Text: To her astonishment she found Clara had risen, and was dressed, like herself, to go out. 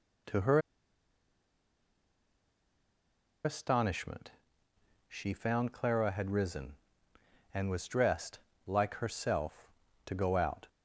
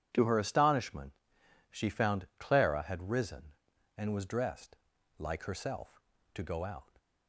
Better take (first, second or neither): second